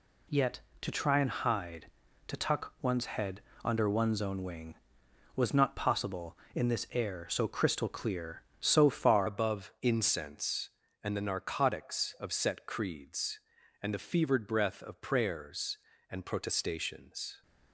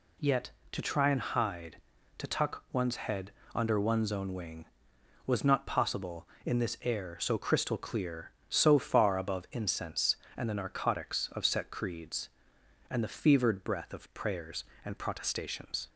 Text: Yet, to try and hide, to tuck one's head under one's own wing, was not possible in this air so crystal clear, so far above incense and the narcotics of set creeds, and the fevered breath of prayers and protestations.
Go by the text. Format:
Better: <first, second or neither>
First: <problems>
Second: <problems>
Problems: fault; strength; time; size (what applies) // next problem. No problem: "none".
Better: second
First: pauses between "head" and "under"; slight; at 3.4 s; 0.22 s long // changes voice at "above"; from 9.2 s on; 8.2 s long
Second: pauses between "head" and "under"; slight; at 3.3 s; 0.22 s long